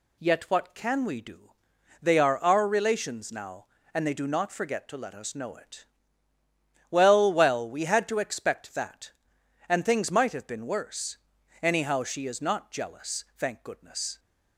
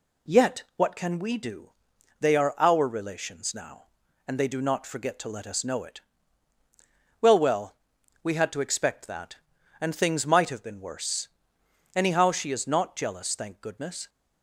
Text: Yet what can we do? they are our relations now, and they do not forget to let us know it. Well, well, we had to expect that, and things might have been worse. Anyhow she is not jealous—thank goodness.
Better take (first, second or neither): neither